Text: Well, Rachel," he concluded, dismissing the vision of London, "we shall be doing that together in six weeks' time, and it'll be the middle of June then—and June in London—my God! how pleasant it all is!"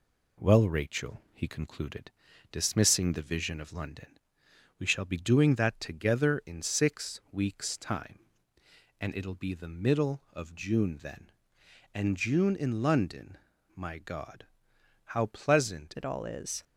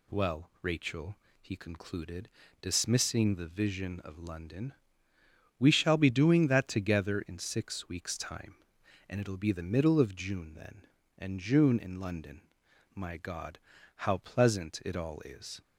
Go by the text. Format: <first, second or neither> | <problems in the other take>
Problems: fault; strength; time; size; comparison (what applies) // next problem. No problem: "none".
second | changes voice at "it"; from 15.9 s on; 0.7 s long